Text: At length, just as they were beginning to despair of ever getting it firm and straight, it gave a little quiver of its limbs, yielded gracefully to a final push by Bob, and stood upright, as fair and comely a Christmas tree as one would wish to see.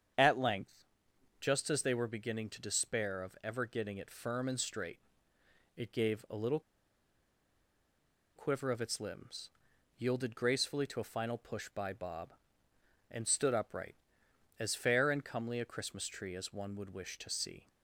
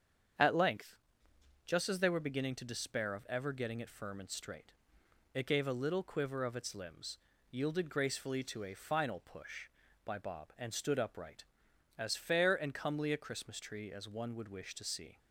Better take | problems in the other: second | starts louder than the rest; strong; until 1.6 s; 7.5 dB; strong in the second // pauses between "little" and "quiver"; strong; at 6.6 s; 1.7 s long

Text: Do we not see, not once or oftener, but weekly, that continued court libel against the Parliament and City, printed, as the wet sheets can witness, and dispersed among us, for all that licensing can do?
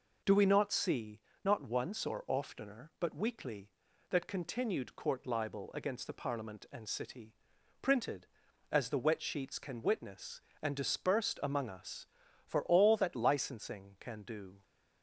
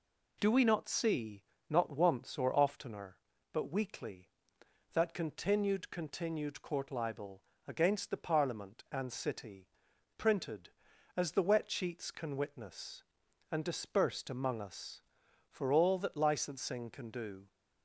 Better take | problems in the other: first | says "continued" twice; at 5.9 s // pauses between "libel" and "against"; slight; at 7.4 s; 0.26 s long

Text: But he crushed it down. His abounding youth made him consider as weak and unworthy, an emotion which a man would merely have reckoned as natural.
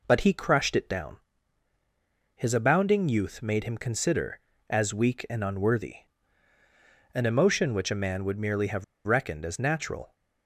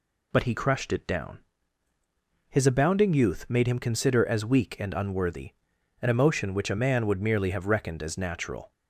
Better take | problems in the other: second | pauses between "have" and "reckoned"; slight; at 8.8 s; 0.22 s long

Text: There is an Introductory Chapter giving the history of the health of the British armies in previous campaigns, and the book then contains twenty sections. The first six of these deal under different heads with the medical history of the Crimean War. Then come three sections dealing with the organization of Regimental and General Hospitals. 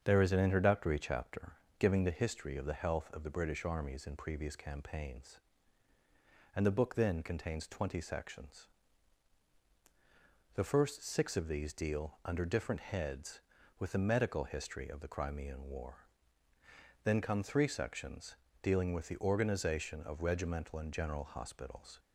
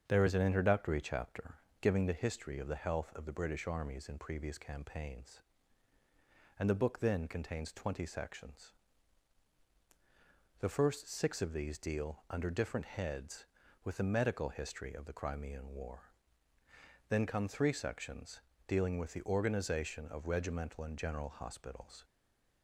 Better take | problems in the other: first | starts louder than the rest; strong; until 1.0 s; 7 dB; strong in the first // pauses between "Chapter" and "giving"; slight; at 1.5 s; 0.26 s long; slight in the first // pauses between "sections" and "dealing"; slight; at 18.4 s; 0.26 s long; slight in the first // stays silent after the last word; slight; from 22.0 s on; 0.6 s long

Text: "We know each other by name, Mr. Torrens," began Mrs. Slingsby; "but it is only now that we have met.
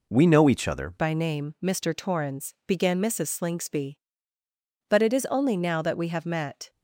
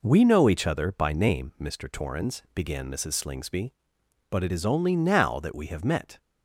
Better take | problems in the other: second | changes voice at "by"; from 0.9 s on; 5.8 s long

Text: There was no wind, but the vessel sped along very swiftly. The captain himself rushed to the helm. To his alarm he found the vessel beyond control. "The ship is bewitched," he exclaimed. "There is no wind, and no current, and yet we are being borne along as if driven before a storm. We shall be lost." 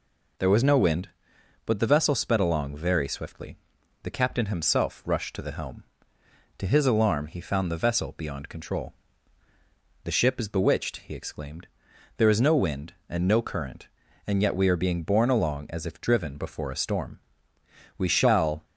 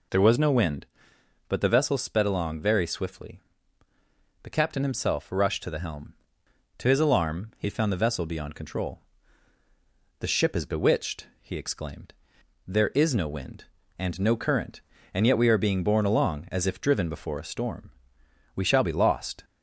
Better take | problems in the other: second | stops before "be lost"; at 18.6 s

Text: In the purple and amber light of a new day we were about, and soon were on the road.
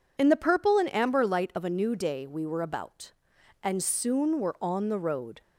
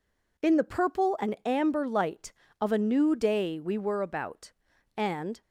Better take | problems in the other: first | stops before "soon were on the road"; at 5.4 s

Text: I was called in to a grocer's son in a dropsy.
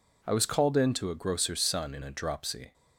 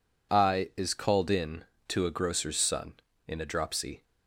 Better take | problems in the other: first | says "is" for "was"; at 0.7 s

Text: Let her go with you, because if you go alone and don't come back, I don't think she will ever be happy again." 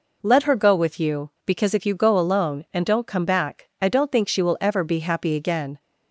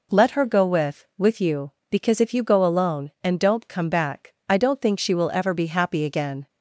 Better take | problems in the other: first | says "with" twice; at 1.1 s

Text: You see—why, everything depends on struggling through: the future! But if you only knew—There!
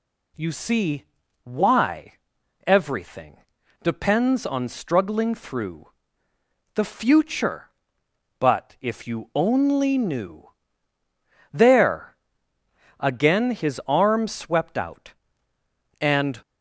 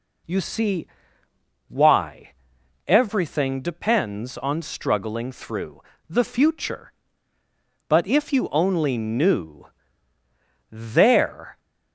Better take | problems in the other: second | pauses between "everything" and "depends"; noticeable; at 3.3 s; 0.46 s long // goes on to say "Again his arm swept out and"; strong; from 12.9 s on; 3.4 s long

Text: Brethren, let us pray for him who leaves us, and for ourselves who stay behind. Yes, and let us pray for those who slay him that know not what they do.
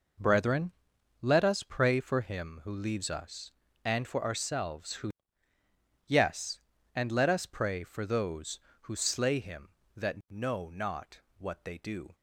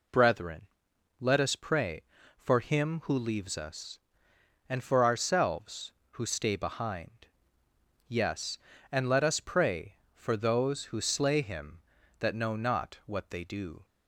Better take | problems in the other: second | skips "stay behind"; at 5.5 s // pauses between "not" and "what"; slight; at 11.2 s; 0.18 s long

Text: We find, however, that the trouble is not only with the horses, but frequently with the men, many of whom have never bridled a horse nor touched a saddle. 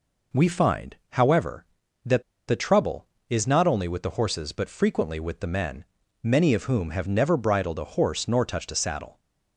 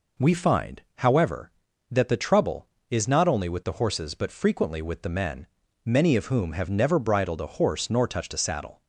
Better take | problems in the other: second | pauses between "that" and "the"; slight; at 2.2 s; 0.25 s long

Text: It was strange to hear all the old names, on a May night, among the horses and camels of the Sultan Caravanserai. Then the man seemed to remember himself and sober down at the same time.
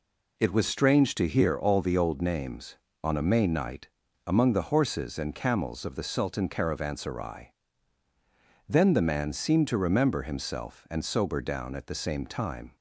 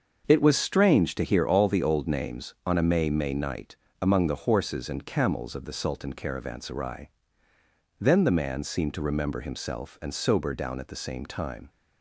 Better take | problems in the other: first | starts louder than the rest; until 1.3 s; 6.5 dB // says "May" twice; at 3.1 s

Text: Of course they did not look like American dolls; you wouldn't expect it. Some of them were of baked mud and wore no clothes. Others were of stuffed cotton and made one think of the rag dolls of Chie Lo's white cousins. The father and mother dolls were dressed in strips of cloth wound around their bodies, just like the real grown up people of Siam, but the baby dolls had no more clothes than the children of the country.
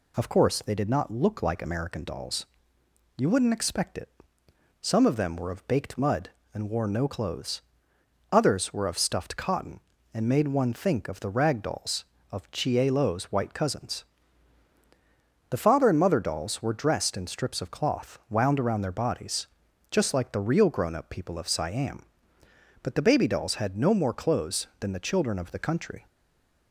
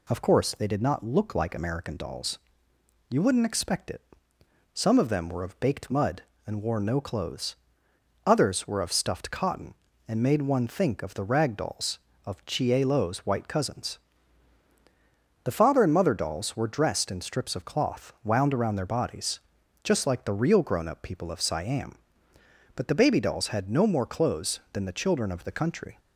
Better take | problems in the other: second | stays silent after the last word; slight; from 26.0 s on; 0.7 s long

